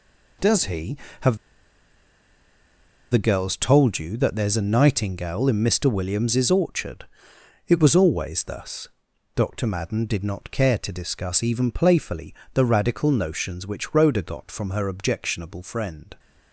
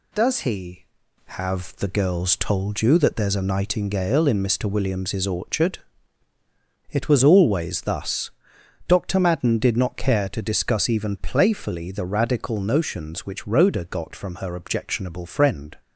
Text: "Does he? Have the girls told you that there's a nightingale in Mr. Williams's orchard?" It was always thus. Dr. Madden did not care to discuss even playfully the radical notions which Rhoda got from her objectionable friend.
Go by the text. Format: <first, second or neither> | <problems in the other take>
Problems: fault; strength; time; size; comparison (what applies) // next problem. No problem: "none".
second | pauses between "Have" and "the"; strong; at 1.3 s; 1.7 s long // pauses between "playfully" and "the"; slight; at 12.3 s; 0.22 s long